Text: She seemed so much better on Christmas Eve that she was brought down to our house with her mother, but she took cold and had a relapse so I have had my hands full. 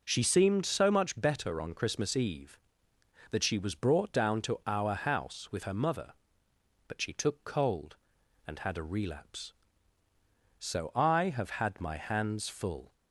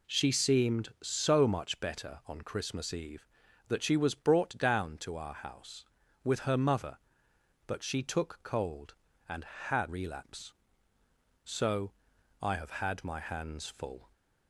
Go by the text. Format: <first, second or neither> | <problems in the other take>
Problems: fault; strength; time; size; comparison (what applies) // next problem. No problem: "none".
first | skips "a"; at 9.8 s // pauses between "so" and "I"; noticeable; at 11.9 s; 0.52 s long